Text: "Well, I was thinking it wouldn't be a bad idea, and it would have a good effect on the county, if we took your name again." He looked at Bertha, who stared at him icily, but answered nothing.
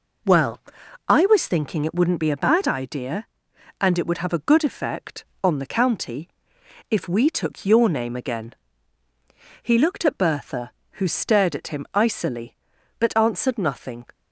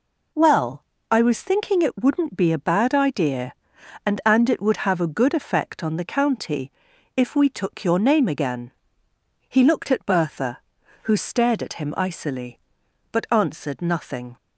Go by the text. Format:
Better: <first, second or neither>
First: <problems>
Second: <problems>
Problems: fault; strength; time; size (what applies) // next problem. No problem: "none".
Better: first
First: none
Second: says "and" twice; at 4.2 s